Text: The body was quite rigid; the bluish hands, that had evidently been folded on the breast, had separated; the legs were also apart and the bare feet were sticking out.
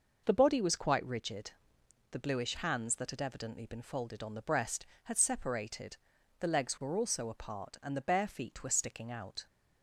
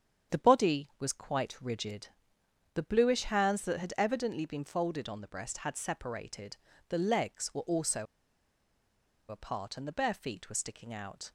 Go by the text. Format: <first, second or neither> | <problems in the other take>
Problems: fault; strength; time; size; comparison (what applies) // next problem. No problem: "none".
first | starts louder than the rest; strong; until 1.4 s; 8 dB // pauses between "also" and "apart"; at 8.0 s; 1.2 s long